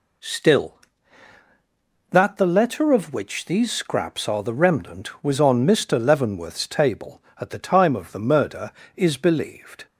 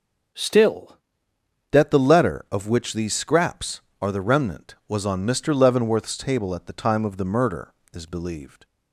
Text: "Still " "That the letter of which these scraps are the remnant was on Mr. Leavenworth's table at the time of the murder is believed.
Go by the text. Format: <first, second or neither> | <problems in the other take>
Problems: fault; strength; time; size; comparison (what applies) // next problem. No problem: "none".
first | changes voice at "That"; from 1.7 s on; 6.9 s long